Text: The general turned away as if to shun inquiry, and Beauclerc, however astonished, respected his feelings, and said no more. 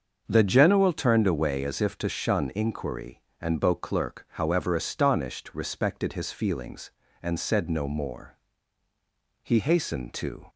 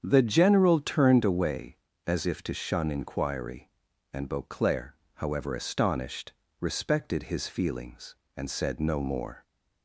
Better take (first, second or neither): second